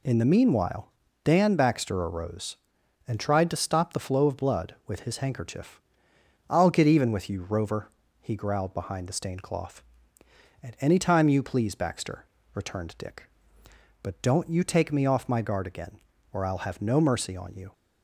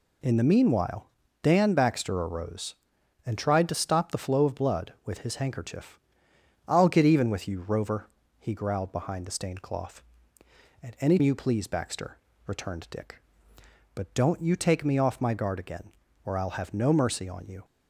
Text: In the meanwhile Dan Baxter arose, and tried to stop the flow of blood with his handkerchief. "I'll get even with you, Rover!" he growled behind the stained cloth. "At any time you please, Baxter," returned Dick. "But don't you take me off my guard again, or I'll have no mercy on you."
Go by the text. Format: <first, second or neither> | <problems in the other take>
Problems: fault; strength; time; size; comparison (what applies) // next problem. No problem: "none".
first | pauses between "meanwhile" and "Dan"; slight; at 1.1 s; 0.32 s long; slight in the first // skips "time"; at 11.1 s